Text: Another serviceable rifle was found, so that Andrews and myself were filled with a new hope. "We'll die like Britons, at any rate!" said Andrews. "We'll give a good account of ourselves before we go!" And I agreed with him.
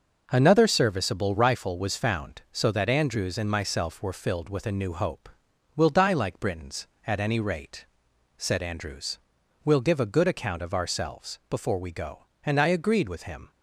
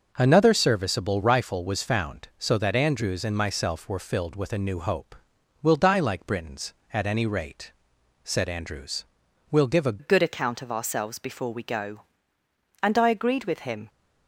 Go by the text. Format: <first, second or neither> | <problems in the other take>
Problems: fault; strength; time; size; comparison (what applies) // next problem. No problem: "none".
first | starts louder than the rest; noticeable; until 1.1 s; 6 dB; noticeable in the first // changes voice at "good"; from 9.9 s on; 3.9 s long